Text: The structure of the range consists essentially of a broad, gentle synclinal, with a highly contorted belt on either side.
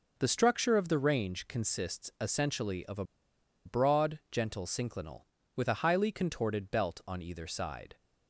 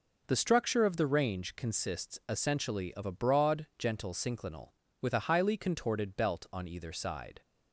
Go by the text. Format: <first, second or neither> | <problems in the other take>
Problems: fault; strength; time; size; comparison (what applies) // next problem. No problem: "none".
second | pauses between "a" and "broad"; noticeable; at 3.0 s; 0.61 s long